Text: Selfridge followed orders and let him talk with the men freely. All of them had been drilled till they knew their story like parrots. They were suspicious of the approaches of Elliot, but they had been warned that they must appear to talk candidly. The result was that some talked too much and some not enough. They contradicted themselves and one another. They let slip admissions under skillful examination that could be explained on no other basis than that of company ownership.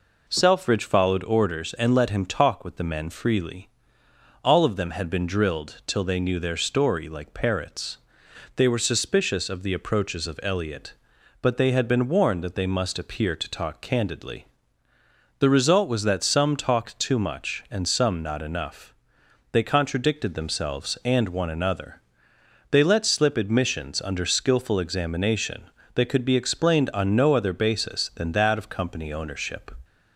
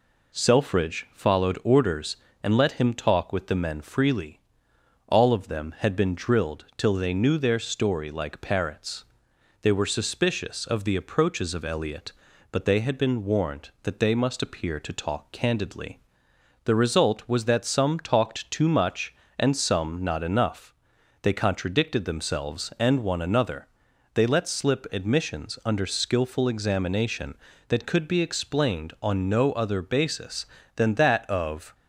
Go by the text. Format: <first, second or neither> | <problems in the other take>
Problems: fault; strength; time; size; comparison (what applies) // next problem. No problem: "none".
first | stops before "company ownership"; at 31.7 s